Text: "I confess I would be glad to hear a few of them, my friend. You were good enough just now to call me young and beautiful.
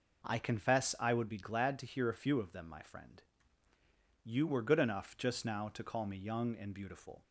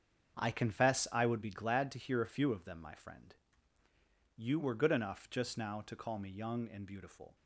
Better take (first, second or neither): first